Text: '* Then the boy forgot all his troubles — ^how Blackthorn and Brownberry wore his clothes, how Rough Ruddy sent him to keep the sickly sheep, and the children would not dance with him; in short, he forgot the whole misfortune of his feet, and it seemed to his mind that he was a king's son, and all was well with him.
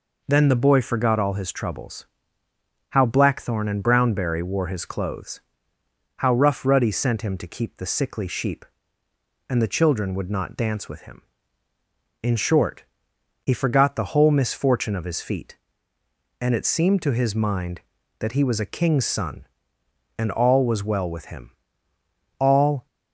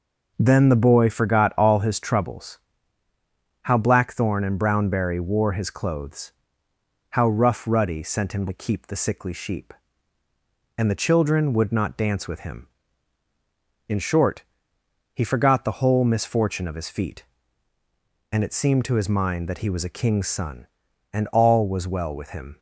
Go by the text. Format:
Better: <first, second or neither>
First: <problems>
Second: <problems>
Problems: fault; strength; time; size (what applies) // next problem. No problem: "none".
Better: second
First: goes on to say "All"; slight; from 22.3 s on; 0.48 s long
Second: none